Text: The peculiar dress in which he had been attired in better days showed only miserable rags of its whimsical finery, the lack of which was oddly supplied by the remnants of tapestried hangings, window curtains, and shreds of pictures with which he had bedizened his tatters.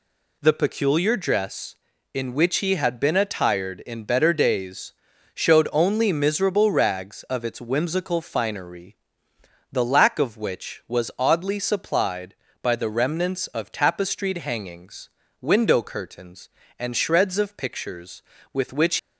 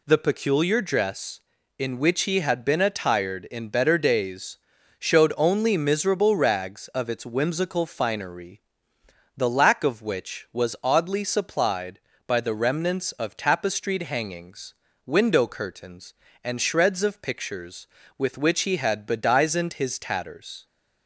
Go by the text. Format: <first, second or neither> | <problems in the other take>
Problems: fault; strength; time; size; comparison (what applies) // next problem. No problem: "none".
second | pauses between "days" and "showed"; at 4.9 s; 0.42 s long; also in the second // stops before "he had bedizened his tatters"; at 18.9 s